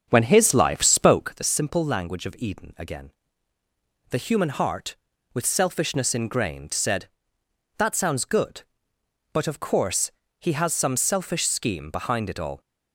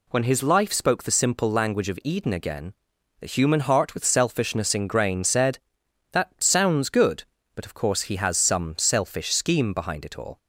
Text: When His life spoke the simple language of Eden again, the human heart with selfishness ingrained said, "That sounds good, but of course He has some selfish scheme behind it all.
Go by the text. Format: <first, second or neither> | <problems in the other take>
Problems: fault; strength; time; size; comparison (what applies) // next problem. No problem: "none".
second | starts louder than the rest; strong; until 1.4 s; 7.5 dB // pauses between "course" and "He"; slight; at 10.1 s; 0.26 s long